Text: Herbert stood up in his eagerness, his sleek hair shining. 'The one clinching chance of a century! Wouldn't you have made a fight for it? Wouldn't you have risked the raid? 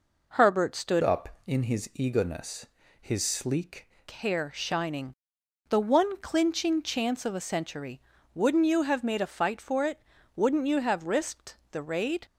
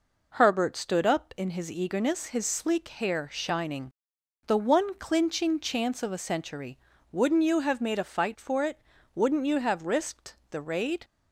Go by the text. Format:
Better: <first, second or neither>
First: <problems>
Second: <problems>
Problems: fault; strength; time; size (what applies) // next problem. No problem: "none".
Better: second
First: changes voice from "up" to "sleek"; from 1.0 to 3.8 s; 2.8 s long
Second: none